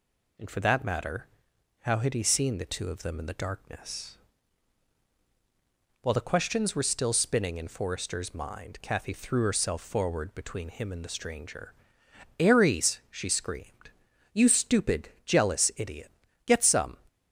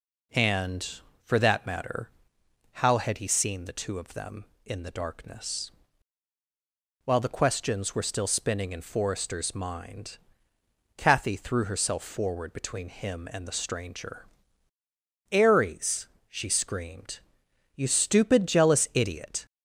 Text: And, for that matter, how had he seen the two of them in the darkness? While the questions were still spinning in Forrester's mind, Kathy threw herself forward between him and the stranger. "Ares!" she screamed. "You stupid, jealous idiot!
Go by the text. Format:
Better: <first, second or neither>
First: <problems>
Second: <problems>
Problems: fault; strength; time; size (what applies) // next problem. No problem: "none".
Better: second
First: goes on to say "Get some"; from 16.4 s on; 0.52 s long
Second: none